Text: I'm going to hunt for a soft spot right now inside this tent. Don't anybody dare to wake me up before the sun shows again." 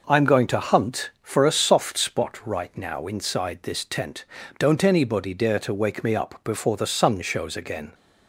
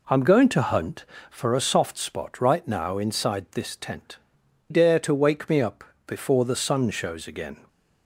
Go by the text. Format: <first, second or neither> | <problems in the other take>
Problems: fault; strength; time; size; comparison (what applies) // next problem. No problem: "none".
first | skips "Don't anybody"; at 4.4 s // pauses between "up" and "before"; slight; at 5.8 s; 0.22 s long